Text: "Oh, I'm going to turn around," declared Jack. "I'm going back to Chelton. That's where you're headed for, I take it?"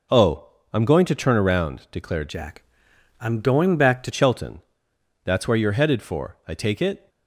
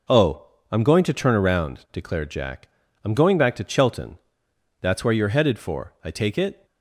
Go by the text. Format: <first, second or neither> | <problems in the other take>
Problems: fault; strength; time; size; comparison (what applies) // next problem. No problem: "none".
second | changes voice from "Jack" to "to"; from 2.2 to 4.1 s; 1.9 s long